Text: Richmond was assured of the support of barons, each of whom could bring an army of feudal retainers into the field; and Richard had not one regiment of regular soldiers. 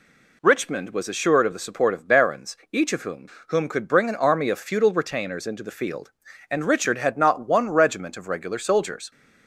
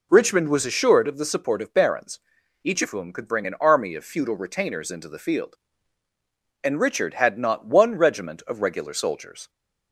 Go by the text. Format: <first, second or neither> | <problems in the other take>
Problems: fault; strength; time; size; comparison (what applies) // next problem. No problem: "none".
second | says "whom" twice; at 3.4 s